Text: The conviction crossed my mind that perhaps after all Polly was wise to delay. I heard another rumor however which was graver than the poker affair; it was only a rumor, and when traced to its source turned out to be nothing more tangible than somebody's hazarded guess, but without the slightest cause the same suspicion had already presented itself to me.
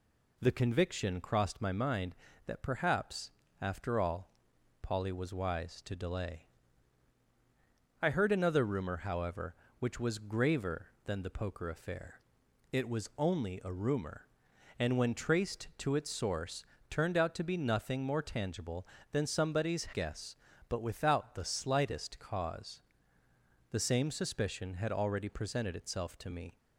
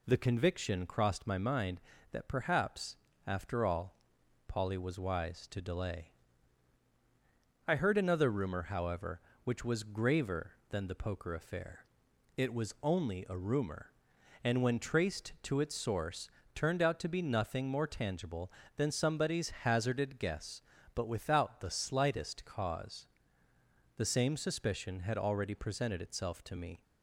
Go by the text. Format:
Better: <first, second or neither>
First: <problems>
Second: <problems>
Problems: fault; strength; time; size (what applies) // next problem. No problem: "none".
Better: second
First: pauses between "perhaps" and "after"; slight; at 3.3 s; 0.28 s long // pauses between "all" and "Polly"; noticeable; at 4.3 s; 0.52 s long // pauses between "source" and "turned"; slight; at 16.6 s; 0.24 s long // skips "hazarded"; at 19.8 s // pauses between "cause" and "the"; noticeable; at 22.8 s; 0.88 s long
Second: pauses between "perhaps" and "after"; slight; at 2.9 s; 0.28 s long // pauses between "all" and "Polly"; noticeable; at 3.9 s; 0.52 s long // pauses between "source" and "turned"; slight; at 16.2 s; 0.24 s long // pauses between "cause" and "the"; noticeable; at 23.0 s; 0.88 s long